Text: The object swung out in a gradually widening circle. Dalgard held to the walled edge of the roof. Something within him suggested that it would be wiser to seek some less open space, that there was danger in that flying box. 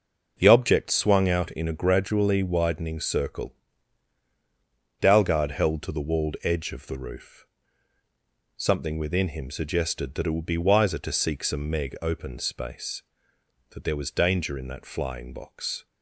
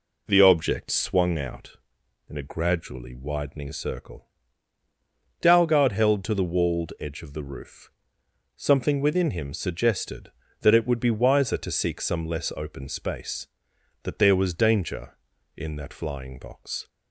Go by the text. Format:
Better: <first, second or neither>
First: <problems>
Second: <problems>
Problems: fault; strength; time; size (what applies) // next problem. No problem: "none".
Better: second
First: says "meg" for "less"; at 11.7 s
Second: none